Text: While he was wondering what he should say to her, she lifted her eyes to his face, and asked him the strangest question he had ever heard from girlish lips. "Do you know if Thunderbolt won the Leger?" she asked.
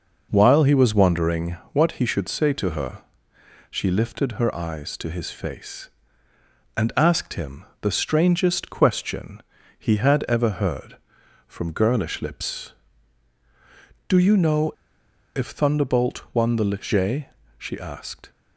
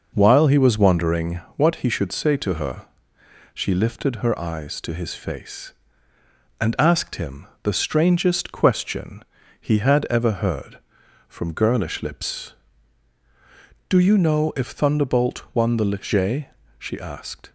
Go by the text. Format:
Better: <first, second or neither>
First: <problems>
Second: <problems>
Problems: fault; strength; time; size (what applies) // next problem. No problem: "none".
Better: second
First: pauses between "wondering" and "what"; slight; at 1.5 s; 0.16 s long // pauses between "him" and "the"; slight; at 7.6 s; 0.16 s long // pauses between "question" and "he"; at 9.4 s; 0.38 s long // pauses between "know" and "if"; noticeable; at 14.7 s; 0.64 s long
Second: pauses between "wondering" and "what"; slight; at 1.4 s; 0.16 s long // pauses between "him" and "the"; slight; at 7.4 s; 0.16 s long // pauses between "question" and "he"; at 9.2 s; 0.38 s long